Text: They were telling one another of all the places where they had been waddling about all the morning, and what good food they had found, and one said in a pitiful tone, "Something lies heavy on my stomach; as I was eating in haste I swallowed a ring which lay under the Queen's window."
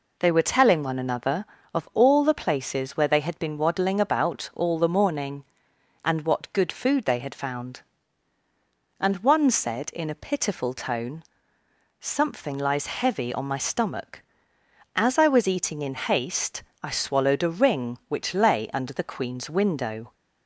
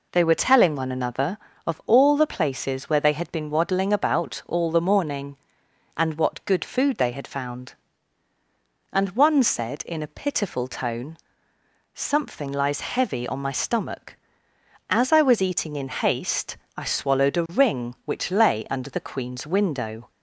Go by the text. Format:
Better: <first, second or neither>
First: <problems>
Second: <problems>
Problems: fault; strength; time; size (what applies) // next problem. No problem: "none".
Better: neither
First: pauses between "haste" and "I"; slight; at 16.6 s; 0.18 s long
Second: pauses between "haste" and "I"; slight; at 16.5 s; 0.18 s long